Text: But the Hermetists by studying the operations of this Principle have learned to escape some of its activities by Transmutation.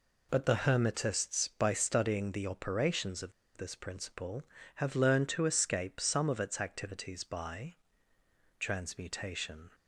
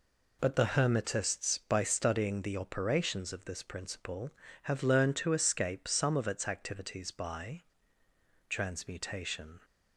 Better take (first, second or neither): second